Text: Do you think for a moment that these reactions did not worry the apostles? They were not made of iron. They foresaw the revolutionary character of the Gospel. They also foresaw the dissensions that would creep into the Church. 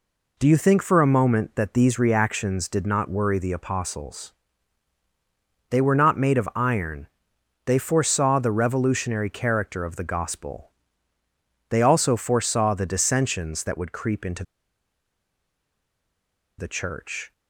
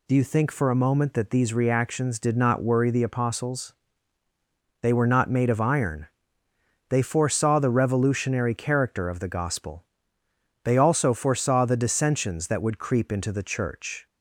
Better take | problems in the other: second | pauses between "into" and "the"; strong; at 14.4 s; 2.1 s long

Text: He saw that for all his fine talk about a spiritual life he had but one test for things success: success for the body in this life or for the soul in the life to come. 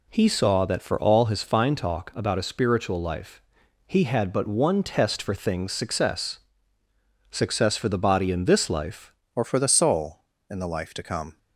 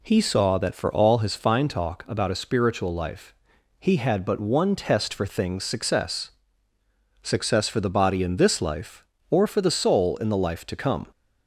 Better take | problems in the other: second | pauses between "life" and "he"; at 3.4 s; 0.44 s long; also in the second // changes voice at "or"; from 9.3 s on; 2.0 s long

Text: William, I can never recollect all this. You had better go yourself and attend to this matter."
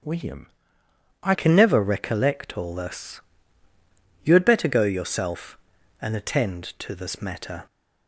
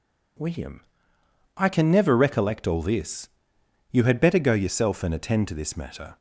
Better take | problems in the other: second | starts louder than the rest; strong; until 1.8 s; 8.5 dB // changes voice at "can"; from 1.3 s on; 6.3 s long

